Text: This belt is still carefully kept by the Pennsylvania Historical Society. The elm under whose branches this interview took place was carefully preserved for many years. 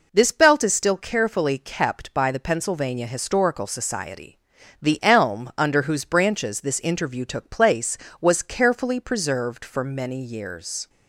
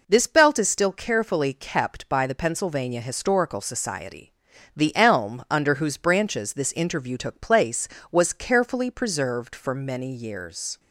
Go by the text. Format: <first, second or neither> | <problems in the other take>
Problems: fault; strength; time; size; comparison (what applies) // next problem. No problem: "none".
neither | none